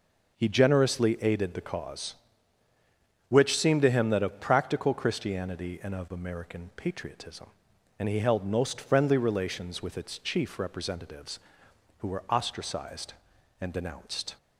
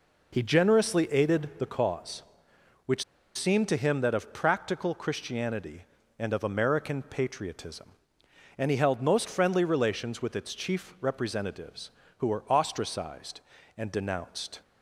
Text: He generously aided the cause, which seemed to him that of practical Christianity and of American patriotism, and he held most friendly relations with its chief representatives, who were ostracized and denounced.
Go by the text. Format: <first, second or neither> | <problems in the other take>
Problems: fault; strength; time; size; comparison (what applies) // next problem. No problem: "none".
first | pauses between "which" and "seemed"; slight; at 3.0 s; 0.31 s long